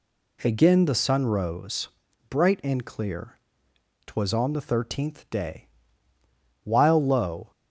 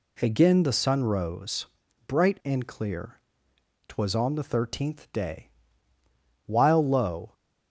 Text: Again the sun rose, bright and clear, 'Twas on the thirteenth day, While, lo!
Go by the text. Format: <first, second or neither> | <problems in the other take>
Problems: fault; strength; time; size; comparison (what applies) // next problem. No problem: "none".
neither | none